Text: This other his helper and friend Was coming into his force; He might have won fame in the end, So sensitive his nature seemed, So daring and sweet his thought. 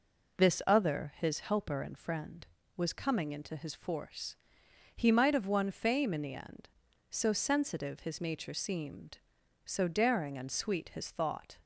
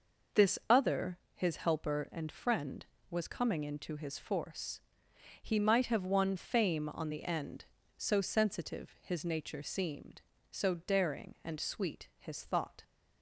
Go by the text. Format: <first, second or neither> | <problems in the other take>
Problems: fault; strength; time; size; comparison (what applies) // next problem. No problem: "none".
first | pauses between "other" and "his"; slight; at 1.1 s; 0.16 s long // says "on" for "in"; at 6.9 s